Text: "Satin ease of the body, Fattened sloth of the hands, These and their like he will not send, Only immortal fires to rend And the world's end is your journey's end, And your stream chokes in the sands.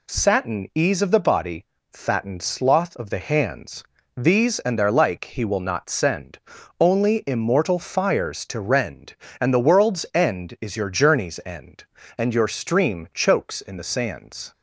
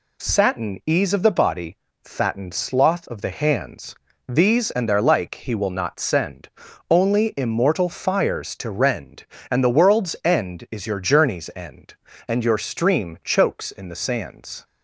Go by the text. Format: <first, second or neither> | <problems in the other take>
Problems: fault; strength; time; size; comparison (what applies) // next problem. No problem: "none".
neither | none